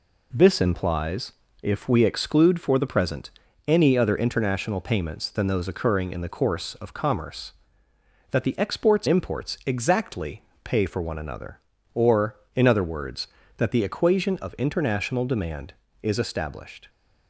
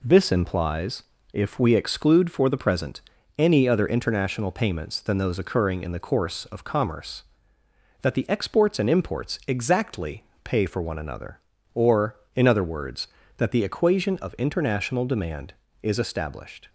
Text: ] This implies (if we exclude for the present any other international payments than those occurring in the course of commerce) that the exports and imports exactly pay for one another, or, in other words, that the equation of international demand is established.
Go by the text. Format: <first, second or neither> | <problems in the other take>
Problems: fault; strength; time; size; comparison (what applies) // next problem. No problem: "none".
second | pauses between "present" and "any"; slight; at 3.3 s; 0.36 s long; slight in the second // skips "and"; at 9.0 s // pauses between "exactly" and "pay"; slight; at 10.4 s; 0.20 s long; slight in the second